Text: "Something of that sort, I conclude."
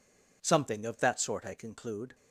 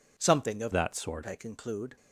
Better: first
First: none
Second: changes voice from "that" to "sort"; from 0.7 to 1.2 s; 0.5 s long

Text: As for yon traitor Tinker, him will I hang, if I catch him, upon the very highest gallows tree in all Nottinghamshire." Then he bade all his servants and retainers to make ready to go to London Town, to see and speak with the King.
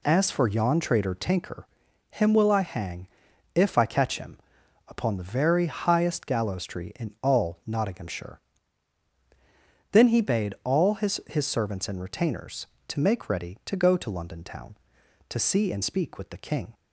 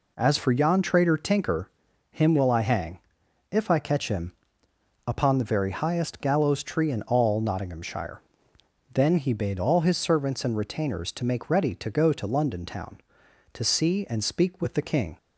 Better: second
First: says "his" twice; at 11.2 s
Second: none

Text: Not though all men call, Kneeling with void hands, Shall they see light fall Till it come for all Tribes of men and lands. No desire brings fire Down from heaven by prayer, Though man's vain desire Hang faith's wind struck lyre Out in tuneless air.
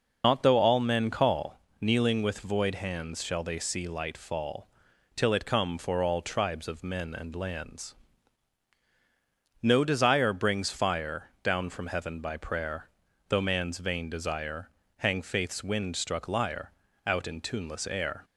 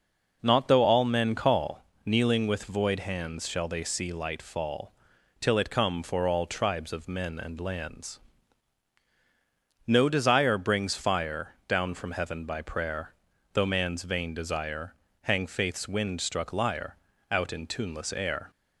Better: second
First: loses the start of "Not"; at 0.2 s; 80 ms // pauses between "fall" and "Till"; noticeable; at 4.6 s; 0.48 s long // pauses between "desire" and "Hang"; slight; at 14.7 s; 0.28 s long // pauses between "lyre" and "Out"; slight; at 16.7 s; 0.34 s long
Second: pauses between "fall" and "Till"; noticeable; at 4.9 s; 0.48 s long // pauses between "desire" and "Hang"; slight; at 14.9 s; 0.28 s long // pauses between "lyre" and "Out"; slight; at 16.9 s; 0.34 s long

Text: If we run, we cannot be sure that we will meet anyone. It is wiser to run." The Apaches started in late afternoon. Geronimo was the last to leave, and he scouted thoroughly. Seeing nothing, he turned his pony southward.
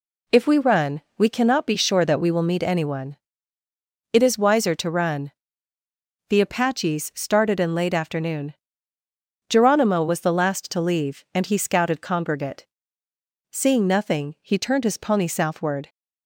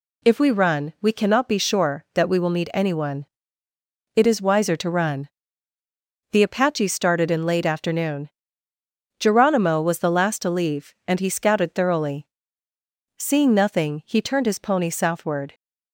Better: second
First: says "congregate" for "thoroughly"; at 12.0 s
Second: none

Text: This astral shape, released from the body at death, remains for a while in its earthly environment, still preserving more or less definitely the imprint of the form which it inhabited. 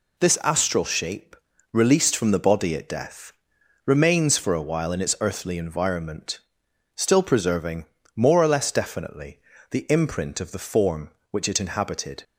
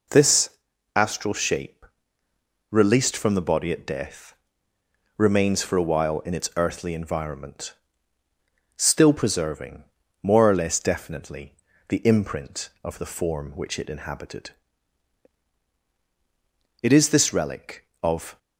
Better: first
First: pauses between "preserving" and "more"; slight; at 7.8 s; 0.30 s long // pauses between "definitely" and "the"; slight; at 9.3 s; 0.30 s long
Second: pauses between "This" and "astral"; noticeable; at 0.4 s; 0.48 s long // pauses between "preserving" and "more"; at 9.8 s; 0.38 s long // pauses between "definitely" and "the"; at 11.5 s; 0.38 s long // goes on to say "It is this relic of"; from 16.8 s on; 1.5 s long

